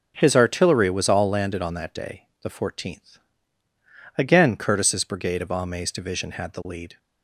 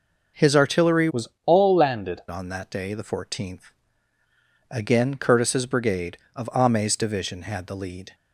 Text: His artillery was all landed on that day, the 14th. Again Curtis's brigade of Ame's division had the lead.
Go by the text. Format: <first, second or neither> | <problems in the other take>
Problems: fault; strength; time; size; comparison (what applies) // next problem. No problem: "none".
first | changes voice from "was" to "landed"; from 1.0 to 2.1 s; 1.1 s long // pauses between "was" and "all"; slight; at 1.2 s; 0.20 s long